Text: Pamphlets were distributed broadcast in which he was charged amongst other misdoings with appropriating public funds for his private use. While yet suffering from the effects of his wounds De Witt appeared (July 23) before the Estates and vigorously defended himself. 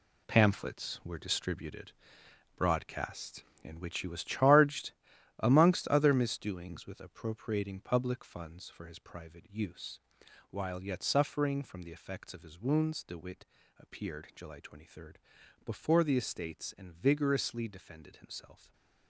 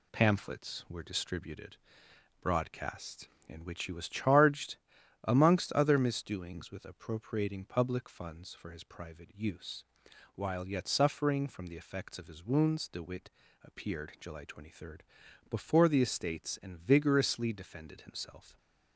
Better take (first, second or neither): second